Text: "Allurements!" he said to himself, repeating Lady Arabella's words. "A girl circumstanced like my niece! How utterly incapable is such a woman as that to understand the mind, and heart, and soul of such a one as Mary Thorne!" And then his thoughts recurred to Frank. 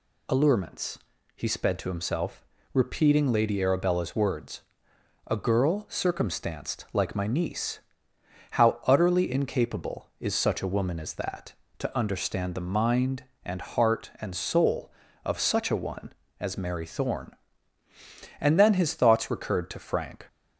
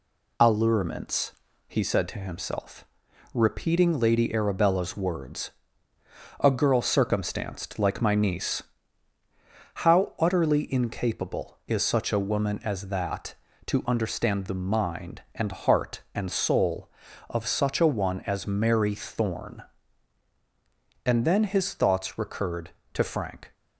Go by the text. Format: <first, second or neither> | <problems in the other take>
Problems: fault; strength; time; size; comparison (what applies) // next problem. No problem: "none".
second | says "sped" for "said"; at 1.4 s